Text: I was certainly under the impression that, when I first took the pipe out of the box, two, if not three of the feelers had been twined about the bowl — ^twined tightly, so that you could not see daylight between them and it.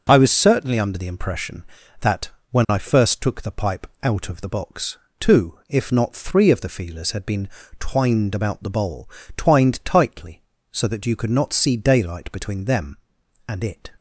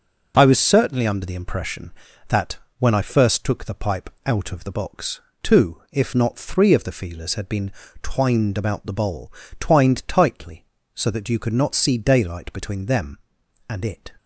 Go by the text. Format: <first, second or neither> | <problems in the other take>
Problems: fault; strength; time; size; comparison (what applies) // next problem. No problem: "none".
neither | pauses between "pipe" and "out"; slight; the same in both // pauses between "been" and "twined"; slight; the same in both